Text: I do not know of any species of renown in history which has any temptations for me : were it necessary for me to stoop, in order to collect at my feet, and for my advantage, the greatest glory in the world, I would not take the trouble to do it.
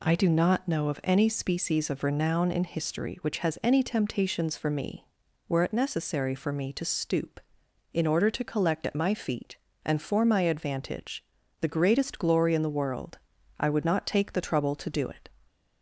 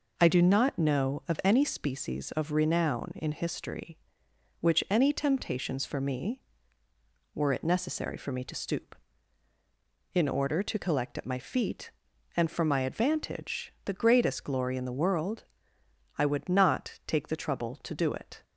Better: first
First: none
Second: skips "has"; at 4.8 s

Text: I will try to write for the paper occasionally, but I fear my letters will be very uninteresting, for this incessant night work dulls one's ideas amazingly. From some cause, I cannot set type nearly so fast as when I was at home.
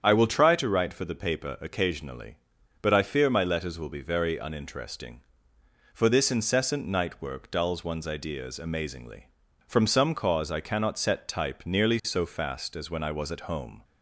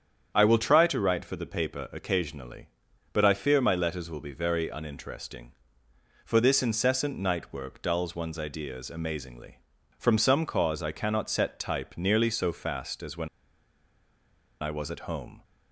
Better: first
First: starts louder than the rest; strong; until 1.0 s; 8 dB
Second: starts louder than the rest; strong; until 1.3 s; 8 dB // pauses between "when" and "I"; strong; at 13.2 s; 1.3 s long

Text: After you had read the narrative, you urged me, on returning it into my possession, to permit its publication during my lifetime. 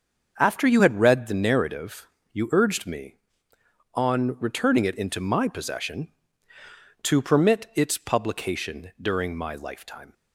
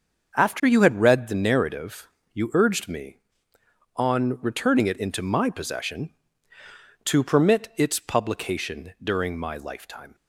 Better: neither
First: starts louder than the rest; until 1.4 s; 6.5 dB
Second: starts louder than the rest; until 1.4 s; 6.5 dB

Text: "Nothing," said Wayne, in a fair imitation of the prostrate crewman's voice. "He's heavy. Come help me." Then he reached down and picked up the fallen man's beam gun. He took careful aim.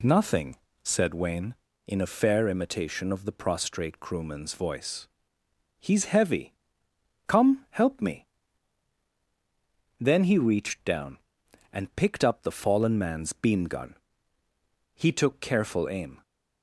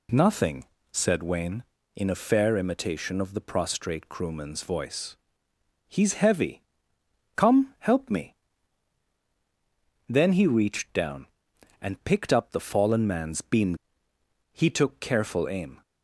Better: first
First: none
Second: skips "gun"; at 14.1 s

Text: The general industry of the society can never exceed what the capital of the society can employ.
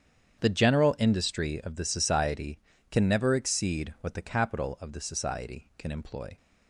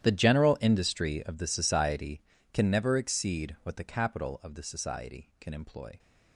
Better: first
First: starts louder than the rest; strong; until 1.4 s; 8.5 dB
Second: gets quieter; strong; throughout; 20.5 dB // starts louder than the rest; strong; until 1.0 s; 11.5 dB

